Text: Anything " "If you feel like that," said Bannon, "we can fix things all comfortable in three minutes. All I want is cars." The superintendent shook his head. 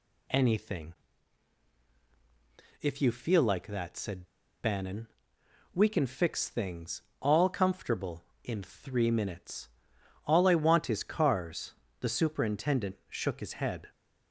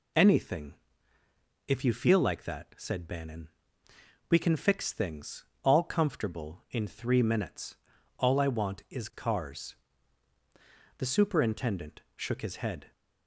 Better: second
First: pauses between "said" and "Bannon"; slight; at 4.2 s; 0.35 s long // pauses between "things" and "all"; slight; at 7.0 s; 0.18 s long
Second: pauses between "things" and "all"; slight; at 5.4 s; 0.20 s long

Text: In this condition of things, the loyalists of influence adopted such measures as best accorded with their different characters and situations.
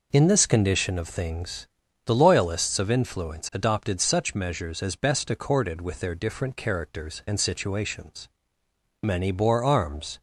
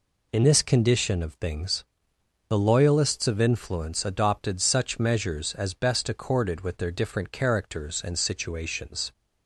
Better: second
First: goes on to say "Many bore arms"; noticeable; from 9.0 s on; 1.1 s long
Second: none

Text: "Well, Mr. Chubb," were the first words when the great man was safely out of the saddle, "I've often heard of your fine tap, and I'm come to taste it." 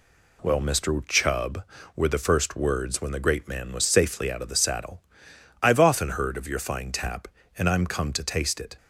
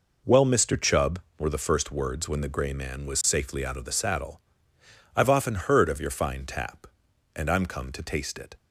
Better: first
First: none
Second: says "grey" for "great"; at 2.4 s

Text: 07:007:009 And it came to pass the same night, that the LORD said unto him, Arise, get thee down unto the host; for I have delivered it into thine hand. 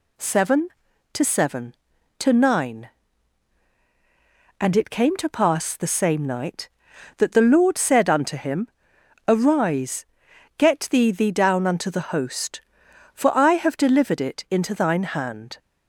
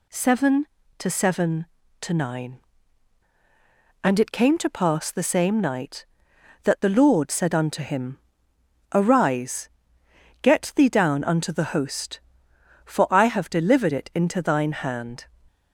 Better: second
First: says "thee" twice; at 11.1 s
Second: none

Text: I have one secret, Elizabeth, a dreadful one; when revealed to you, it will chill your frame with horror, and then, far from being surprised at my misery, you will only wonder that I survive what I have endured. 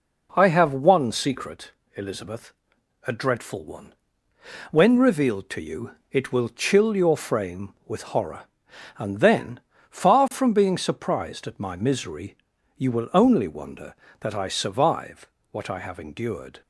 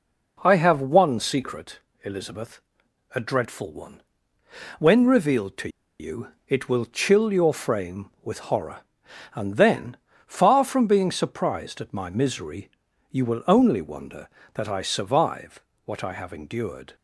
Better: first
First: pauses between "survive" and "what"; slight; at 15.2 s; 0.22 s long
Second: pauses between "to" and "you"; slight; at 5.6 s; 0.31 s long // pauses between "survive" and "what"; slight; at 15.6 s; 0.22 s long

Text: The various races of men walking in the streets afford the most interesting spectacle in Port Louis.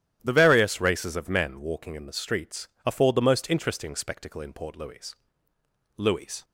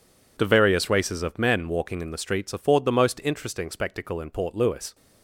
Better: second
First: starts louder than the rest; strong; until 1.2 s; 11.5 dB // pauses between "streets" and "afford"; slight; at 2.6 s; 0.16 s long // says "Louis" twice; at 5.9 s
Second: none

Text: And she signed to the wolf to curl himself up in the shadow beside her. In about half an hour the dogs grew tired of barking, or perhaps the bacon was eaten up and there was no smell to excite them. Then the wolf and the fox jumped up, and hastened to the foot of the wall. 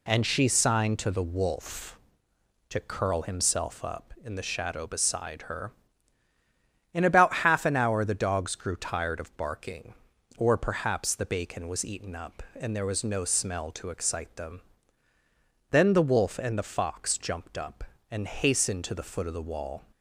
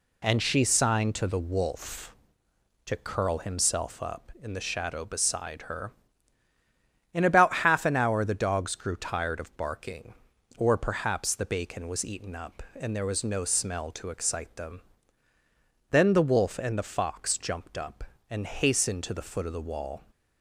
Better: neither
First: none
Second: none

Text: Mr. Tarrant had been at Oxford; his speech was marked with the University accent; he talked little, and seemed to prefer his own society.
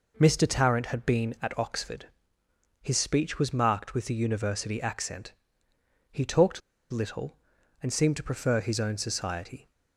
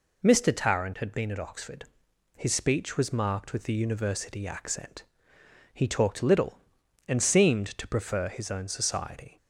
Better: second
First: pauses between "talked" and "little"; slight; at 6.6 s; 0.31 s long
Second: none

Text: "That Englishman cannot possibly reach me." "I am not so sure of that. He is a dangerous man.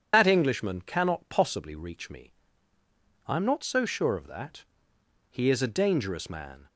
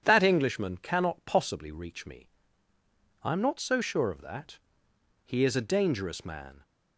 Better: second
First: loses the start of "That"; at 0.1 s; 65 ms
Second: none

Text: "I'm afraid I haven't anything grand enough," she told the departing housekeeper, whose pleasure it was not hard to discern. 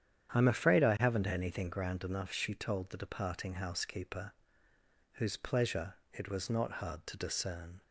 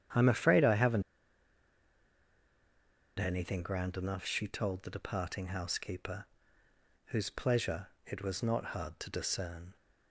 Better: first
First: starts louder than the rest; strong; until 1.3 s; 9.5 dB // pauses between "pleasure" and "it"; slight; at 5.9 s; 0.16 s long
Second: starts louder than the rest; strong; until 3.3 s; 9 dB // pauses between "haven't" and "anything"; strong; at 1.0 s; 2.1 s long // pauses between "pleasure" and "it"; slight; at 7.8 s; 0.16 s long

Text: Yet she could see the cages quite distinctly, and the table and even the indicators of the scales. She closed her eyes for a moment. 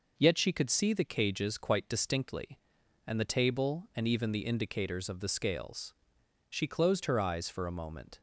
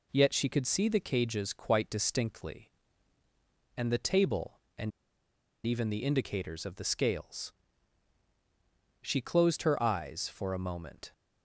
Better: first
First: none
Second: pauses between "and" and "even"; noticeable; at 4.9 s; 0.75 s long

